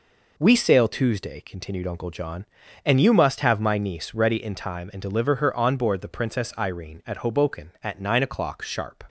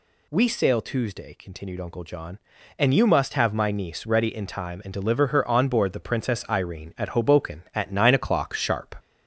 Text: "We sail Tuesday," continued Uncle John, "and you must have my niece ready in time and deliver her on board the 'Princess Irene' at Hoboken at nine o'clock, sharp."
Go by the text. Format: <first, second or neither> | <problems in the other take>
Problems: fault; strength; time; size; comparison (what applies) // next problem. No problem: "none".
first | gets louder; slight; throughout; 2.5 dB